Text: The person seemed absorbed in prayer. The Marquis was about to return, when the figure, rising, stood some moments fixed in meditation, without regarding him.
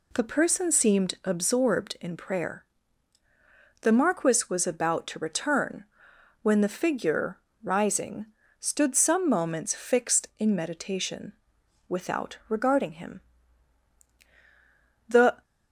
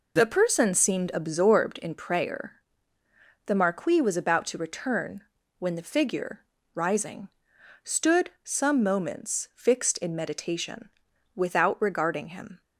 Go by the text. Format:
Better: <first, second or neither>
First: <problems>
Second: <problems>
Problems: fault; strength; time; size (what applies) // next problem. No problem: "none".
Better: second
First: goes on to say "The"; slight; from 15.0 s on; 0.34 s long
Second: none